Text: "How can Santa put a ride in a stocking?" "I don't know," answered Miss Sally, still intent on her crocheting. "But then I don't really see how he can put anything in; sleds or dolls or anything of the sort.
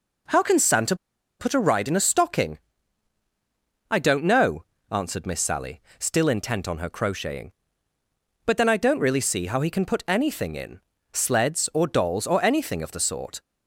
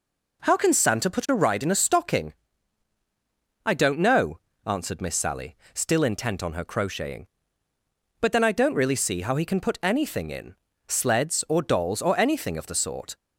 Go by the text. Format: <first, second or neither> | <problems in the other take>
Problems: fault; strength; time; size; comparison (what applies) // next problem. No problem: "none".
second | pauses between "Santa" and "put"; at 0.9 s; 0.44 s long